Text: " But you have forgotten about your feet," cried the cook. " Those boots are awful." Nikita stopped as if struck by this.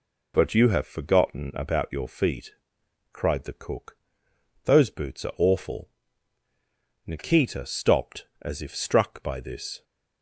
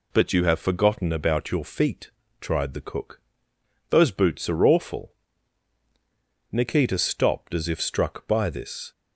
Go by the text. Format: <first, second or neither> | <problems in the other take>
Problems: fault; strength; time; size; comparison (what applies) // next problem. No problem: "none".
first | says "tried" for "cried"; at 2.4 s